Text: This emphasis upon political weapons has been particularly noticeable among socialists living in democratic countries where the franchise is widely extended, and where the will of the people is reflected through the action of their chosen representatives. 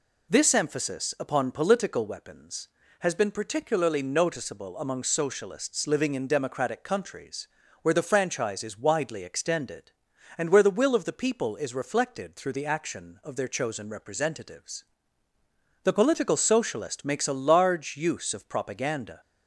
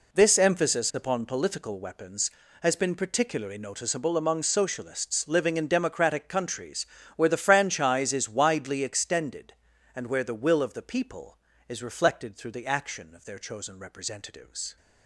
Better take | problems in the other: second | pauses between "countries" and "where"; slight; at 7.4 s; 0.34 s long; slight in the second // goes on to say "The political socialist makes a large use of propaganda"; strong; from 15.8 s on; 3.3 s long

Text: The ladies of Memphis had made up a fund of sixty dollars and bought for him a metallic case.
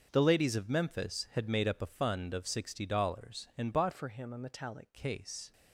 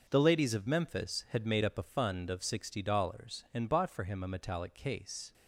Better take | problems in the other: second | starts louder than the rest; until 1.1 s; 6.5 dB // changes voice from "for" to "metallic"; from 3.9 to 4.9 s; 1.0 s long

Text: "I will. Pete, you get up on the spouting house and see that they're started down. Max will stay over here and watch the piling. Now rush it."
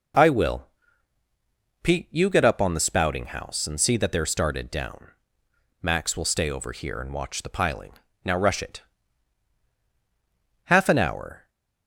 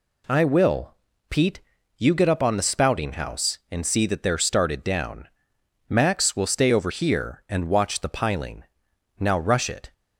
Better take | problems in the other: second | goes on to say "Half an hour"; noticeable; from 10.6 s on; 0.82 s long

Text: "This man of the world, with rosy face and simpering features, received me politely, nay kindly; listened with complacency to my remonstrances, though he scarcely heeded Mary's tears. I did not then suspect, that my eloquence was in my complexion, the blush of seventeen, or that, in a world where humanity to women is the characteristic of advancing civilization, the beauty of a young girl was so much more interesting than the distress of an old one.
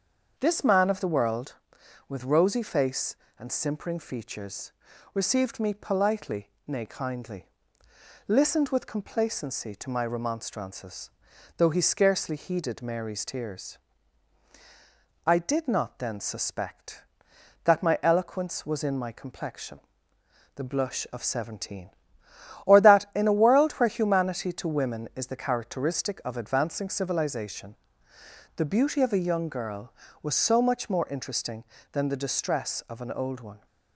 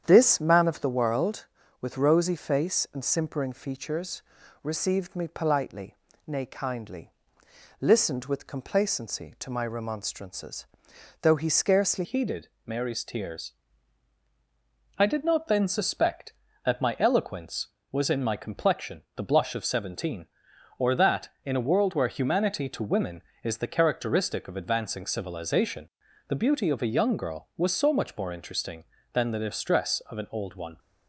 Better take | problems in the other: first | starts louder than the rest; strong; until 1.0 s; 9 dB; also in the first // changes voice at "heeded"; from 12.0 s on; 18.7 s long // pauses between "heeded" and "Mary's"; slight; at 12.4 s; 0.18 s long

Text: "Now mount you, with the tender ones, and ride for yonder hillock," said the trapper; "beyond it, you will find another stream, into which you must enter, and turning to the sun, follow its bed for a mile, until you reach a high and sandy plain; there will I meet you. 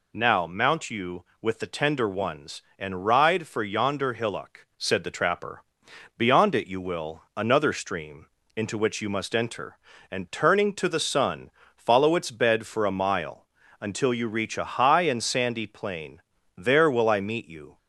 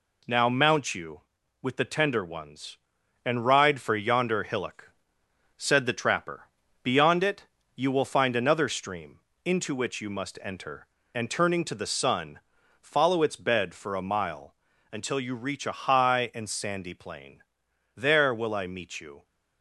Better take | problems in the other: second | skips "find"; at 7.3 s

